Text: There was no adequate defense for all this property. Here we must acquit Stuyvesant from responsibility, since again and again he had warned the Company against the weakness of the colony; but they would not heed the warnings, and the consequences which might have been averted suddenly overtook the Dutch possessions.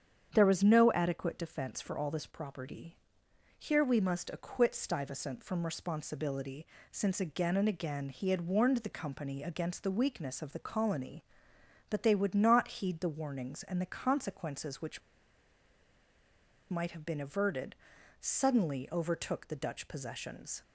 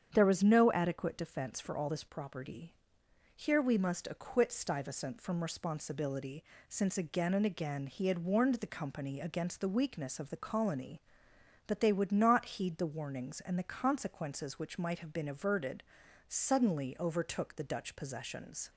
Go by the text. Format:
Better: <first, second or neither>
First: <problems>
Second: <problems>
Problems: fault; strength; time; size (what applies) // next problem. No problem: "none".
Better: second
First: starts louder than the rest; strong; until 1.3 s; 8 dB // pauses between "which" and "might"; strong; at 15.0 s; 1.6 s long // pauses between "averted" and "suddenly"; at 17.7 s; 0.44 s long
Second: starts louder than the rest; strong; until 1.1 s; 8 dB // pauses between "averted" and "suddenly"; at 15.8 s; 0.44 s long